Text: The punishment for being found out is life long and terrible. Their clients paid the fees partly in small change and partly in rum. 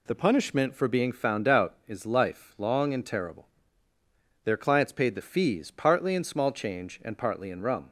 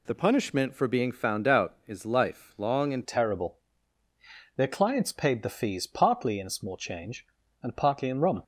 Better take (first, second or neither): first